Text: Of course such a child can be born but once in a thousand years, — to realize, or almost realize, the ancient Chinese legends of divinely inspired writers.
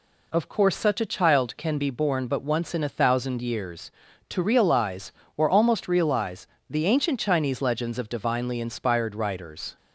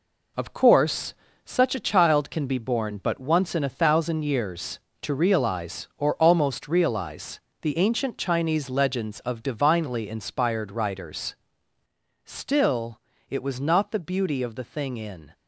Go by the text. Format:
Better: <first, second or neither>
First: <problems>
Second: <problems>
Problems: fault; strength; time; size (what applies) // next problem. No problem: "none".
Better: first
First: none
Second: pauses between "course" and "such"; slight; at 1.1 s; 0.30 s long // goes on to say "Still it was not the beauty of the thing in"; strong; from 12.2 s on; 3.0 s long